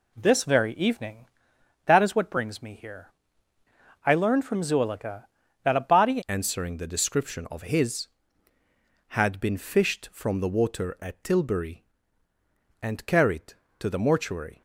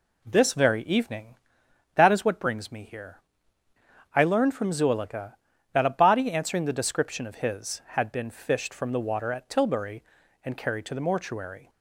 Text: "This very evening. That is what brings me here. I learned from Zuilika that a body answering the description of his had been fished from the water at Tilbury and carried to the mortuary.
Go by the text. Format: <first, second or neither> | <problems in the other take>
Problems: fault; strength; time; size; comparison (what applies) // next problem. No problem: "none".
second | changes voice at "answering"; from 6.2 s on; 8.4 s long